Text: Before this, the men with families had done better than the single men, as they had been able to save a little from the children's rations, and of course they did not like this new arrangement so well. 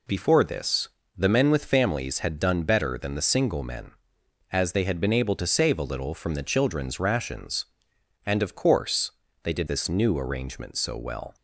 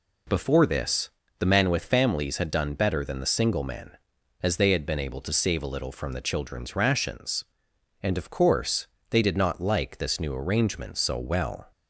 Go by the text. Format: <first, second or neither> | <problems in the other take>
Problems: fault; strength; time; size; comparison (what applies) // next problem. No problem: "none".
second | pauses between "course" and "they"; slight; at 9.1 s; 0.32 s long; slight in the second // skips "not like"; at 9.6 s